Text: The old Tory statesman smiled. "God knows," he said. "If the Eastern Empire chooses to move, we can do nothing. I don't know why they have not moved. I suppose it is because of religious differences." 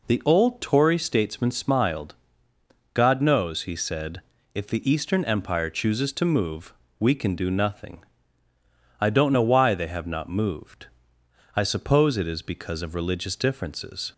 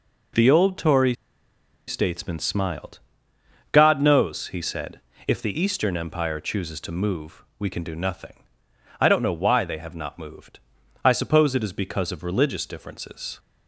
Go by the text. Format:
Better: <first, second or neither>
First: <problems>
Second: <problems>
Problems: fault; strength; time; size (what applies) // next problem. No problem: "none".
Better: first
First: none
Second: pauses between "Tory" and "statesman"; noticeable; at 1.1 s; 0.73 s long